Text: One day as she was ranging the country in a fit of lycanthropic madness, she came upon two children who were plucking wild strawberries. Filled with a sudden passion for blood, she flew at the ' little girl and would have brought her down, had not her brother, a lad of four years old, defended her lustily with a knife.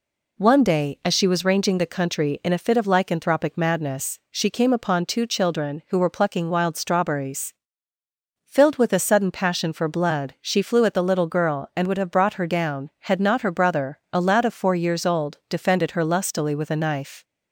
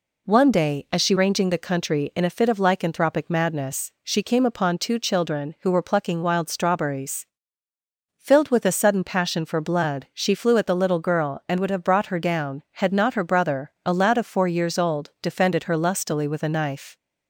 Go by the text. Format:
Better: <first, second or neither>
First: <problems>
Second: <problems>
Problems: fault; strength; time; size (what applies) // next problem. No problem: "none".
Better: first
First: none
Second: skips "was"; at 1.1 s